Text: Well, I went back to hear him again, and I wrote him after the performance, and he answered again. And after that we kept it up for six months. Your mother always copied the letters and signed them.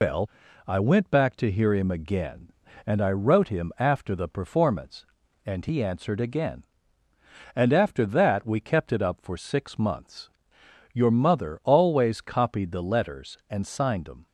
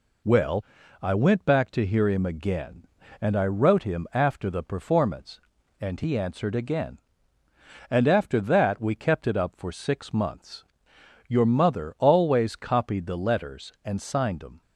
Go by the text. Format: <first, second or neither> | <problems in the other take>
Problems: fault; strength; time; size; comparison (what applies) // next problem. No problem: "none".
second | loses the start of "Well"; at 0.0 s; 110 ms